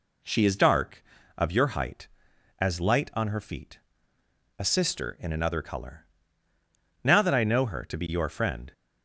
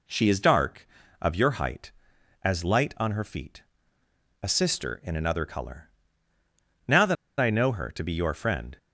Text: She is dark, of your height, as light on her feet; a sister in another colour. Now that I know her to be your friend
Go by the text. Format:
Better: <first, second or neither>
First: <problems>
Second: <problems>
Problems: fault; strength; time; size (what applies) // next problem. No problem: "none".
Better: first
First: none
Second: pauses between "that" and "I"; slight; at 7.1 s; 0.24 s long